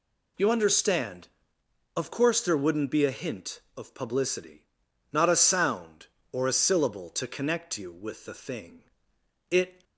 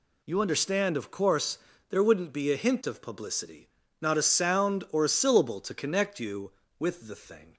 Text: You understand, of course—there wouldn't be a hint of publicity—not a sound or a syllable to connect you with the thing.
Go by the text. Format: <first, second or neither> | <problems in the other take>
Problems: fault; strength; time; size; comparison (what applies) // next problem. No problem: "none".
second | goes on to say "It"; slight; from 9.5 s on; 0.32 s long